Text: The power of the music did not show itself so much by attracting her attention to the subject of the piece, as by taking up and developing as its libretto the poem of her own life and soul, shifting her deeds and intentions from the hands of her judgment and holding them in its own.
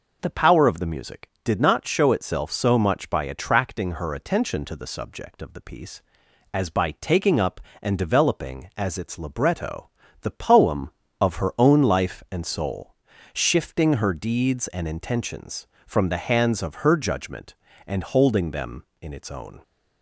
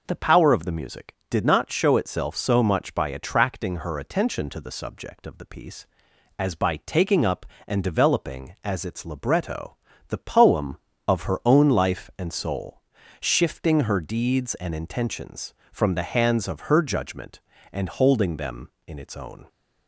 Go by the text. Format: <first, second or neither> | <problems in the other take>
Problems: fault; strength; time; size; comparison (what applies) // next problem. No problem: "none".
neither | pauses between "libretto" and "the"; slight; the same in both